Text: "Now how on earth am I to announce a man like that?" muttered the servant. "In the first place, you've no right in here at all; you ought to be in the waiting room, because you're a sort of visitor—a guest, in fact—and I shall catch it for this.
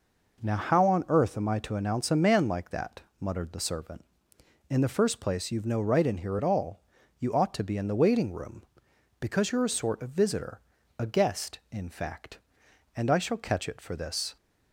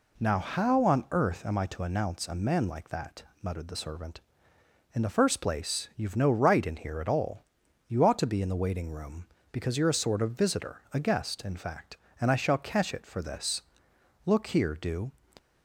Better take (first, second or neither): first